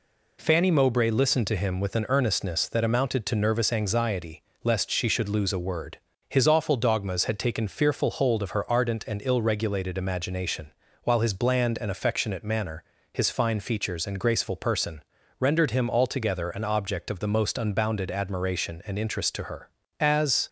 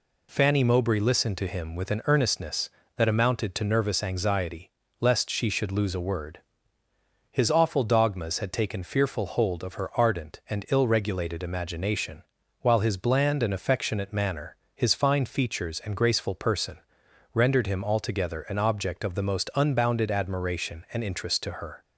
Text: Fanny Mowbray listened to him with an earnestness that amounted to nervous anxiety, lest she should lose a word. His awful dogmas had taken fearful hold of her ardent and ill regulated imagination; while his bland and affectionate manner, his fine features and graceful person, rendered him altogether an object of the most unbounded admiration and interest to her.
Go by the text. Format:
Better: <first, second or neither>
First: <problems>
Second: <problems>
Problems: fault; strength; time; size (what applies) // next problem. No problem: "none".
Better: second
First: goes on to say "As"; slight; from 19.9 s on; 0.48 s long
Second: none